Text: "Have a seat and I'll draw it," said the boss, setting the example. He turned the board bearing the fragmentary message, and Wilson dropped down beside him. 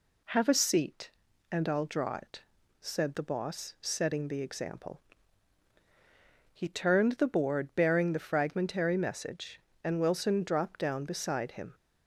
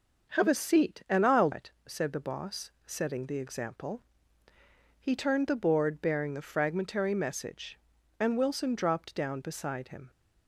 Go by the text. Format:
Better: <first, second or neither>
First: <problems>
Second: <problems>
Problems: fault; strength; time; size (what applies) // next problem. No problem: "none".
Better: first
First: none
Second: skips "draw"; at 1.5 s